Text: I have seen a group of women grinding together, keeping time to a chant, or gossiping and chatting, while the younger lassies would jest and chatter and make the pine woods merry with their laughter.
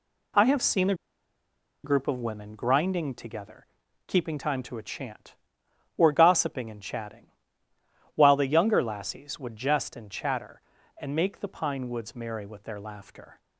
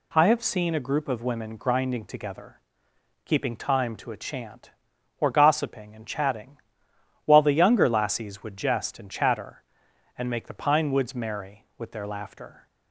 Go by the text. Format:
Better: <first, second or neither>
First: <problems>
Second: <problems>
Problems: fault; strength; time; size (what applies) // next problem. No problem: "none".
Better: second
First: pauses between "a" and "group"; noticeable; at 0.9 s; 0.89 s long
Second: none